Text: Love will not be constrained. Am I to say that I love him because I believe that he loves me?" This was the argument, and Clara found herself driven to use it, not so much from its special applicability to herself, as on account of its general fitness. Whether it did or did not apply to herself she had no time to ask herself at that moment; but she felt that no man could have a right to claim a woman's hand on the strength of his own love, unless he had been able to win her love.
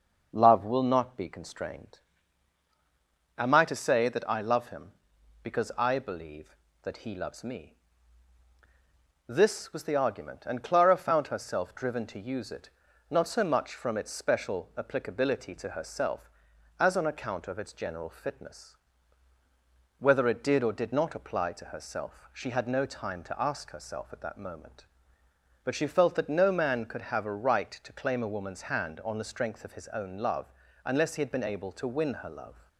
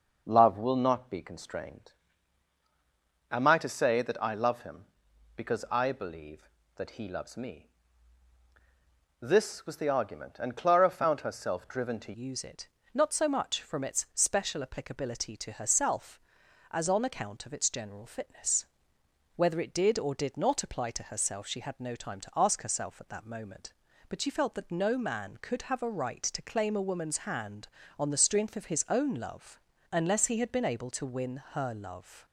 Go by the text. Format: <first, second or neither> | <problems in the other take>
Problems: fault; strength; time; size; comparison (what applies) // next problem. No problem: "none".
first | changes voice at "use"; from 12.1 s on; 20.1 s long